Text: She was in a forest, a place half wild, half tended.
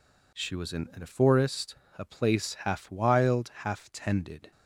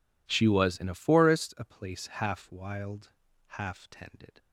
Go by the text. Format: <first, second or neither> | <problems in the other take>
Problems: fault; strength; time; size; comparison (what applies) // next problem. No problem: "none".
second | says "in" twice; at 0.9 s